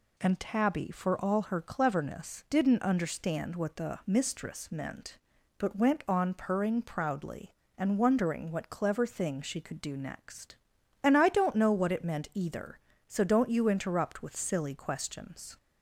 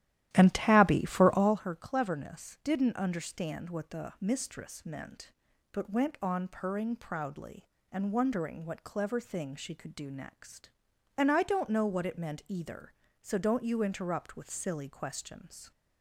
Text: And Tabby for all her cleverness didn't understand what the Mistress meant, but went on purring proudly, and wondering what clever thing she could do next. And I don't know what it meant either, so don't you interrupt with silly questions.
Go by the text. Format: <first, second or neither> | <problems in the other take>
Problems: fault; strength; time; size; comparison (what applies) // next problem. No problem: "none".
first | starts louder than the rest; strong; until 1.7 s; 13 dB